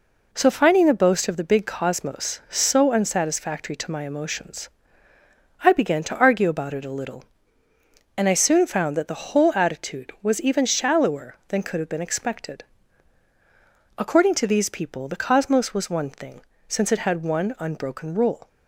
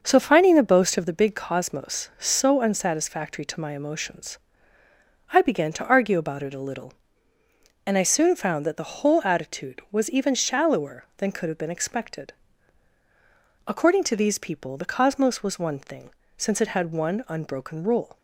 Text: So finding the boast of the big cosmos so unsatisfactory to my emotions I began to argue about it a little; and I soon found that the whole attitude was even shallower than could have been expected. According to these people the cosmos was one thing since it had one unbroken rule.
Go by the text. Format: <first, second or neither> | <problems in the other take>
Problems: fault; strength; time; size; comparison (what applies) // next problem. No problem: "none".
first | starts louder than the rest; until 1.2 s; 6 dB // pauses between "emotions" and "I"; noticeable; at 4.3 s; 0.92 s long; noticeable in the first // pauses between "thing" and "since"; slight; at 16.0 s; 0.26 s long; slight in the first